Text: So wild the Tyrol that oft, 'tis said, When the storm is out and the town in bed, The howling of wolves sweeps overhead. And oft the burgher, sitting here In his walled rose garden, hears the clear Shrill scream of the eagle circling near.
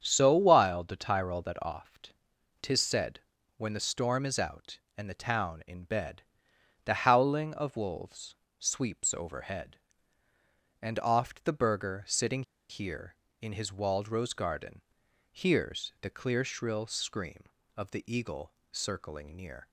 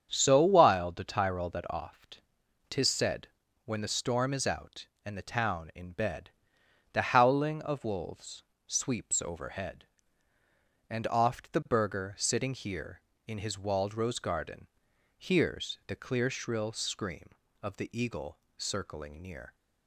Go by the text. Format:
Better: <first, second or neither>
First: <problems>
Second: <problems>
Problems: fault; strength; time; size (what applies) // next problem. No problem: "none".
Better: second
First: starts louder than the rest; strong; until 1.0 s; 8 dB // pauses between "wolves" and "sweeps"; slight; at 8.3 s; 0.24 s long // pauses between "sitting" and "here"; slight; at 12.4 s; 0.27 s long // pauses between "eagle" and "circling"; slight; at 18.5 s; 0.22 s long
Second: starts louder than the rest; strong; until 1.1 s; 8 dB // pauses between "wolves" and "sweeps"; slight; at 8.4 s; 0.24 s long // pauses between "eagle" and "circling"; slight; at 18.3 s; 0.22 s long